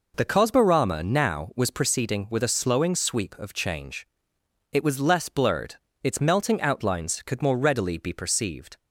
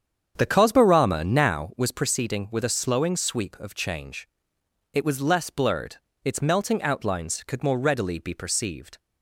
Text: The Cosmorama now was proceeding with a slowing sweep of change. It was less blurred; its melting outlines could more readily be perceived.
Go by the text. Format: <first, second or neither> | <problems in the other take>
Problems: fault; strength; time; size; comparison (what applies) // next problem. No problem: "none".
first | starts louder than the rest; strong; until 1.7 s; 8 dB